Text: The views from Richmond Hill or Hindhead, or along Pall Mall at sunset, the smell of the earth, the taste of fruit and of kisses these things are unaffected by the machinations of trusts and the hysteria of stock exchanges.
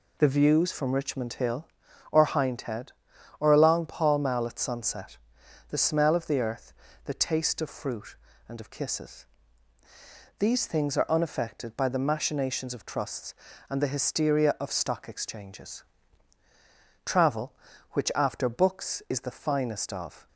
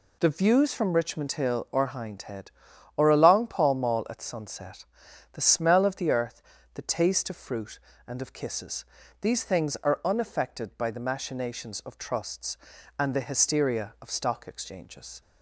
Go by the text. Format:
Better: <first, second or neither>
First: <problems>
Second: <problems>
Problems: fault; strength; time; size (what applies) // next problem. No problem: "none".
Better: second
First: pauses between "kisses" and "these"; at 9.2 s; 1.1 s long // goes on to say "Travel which after books is the finest of"; strong; from 17.0 s on; 3.2 s long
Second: pauses between "kisses" and "these"; slight; at 8.8 s; 0.34 s long